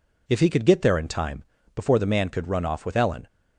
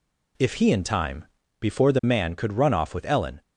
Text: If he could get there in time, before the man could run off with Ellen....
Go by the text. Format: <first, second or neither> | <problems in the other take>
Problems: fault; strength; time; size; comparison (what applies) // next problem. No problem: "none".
first | skips "could get there"; at 0.7 s